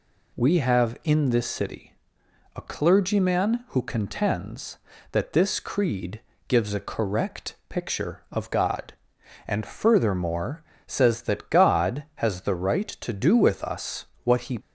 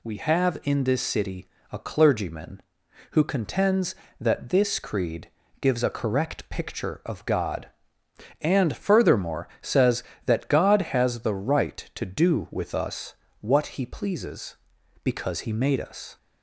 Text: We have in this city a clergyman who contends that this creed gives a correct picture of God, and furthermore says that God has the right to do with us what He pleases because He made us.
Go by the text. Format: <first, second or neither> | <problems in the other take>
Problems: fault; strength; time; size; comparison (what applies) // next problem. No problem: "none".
second | pauses between "city" and "a"; noticeable; at 1.9 s; 0.60 s long; slight in the second // pauses between "creed" and "gives"; slight; at 6.2 s; 0.26 s long; slight in the second // pauses between "furthermore" and "says"; slight; at 10.6 s; 0.24 s long // pauses between "us" and "what"; slight; at 14.0 s; 0.18 s long; slight in the second // stops before "pleases because He made us"; at 14.6 s